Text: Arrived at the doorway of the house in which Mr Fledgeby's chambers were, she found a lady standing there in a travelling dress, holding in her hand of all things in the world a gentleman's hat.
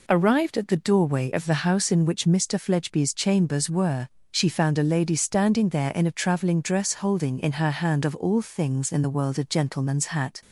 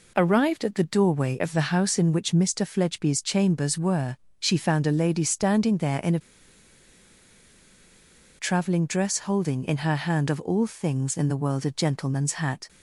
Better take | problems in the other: first | pauses between "a" and "travelling"; strong; at 6.1 s; 2.1 s long

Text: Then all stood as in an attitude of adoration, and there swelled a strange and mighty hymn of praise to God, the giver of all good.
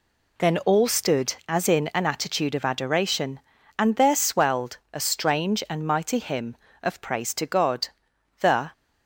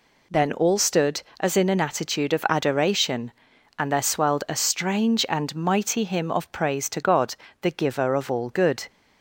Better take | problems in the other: second | pauses between "swelled" and "a"; slight; at 4.7 s; 0.16 s long // stops before "giver of all good"; at 8.7 s

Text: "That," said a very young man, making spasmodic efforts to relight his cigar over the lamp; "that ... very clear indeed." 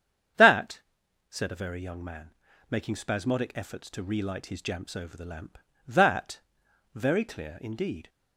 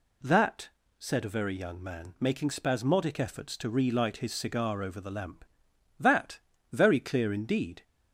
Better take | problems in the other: second | starts louder than the rest; strong; until 1.8 s; 8.5 dB // says "jamps" for "cigar"; at 4.6 s

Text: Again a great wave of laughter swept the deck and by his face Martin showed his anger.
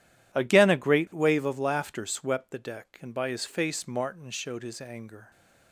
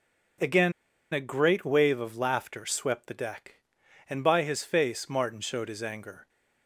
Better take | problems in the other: first | pauses between "Again" and "a"; at 0.7 s; 0.40 s long

